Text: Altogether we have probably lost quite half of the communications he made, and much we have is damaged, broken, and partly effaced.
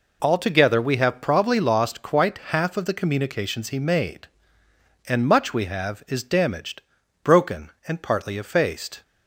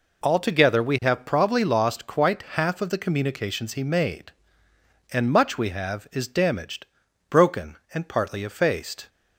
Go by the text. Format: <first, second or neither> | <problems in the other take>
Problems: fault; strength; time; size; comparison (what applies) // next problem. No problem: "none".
neither | none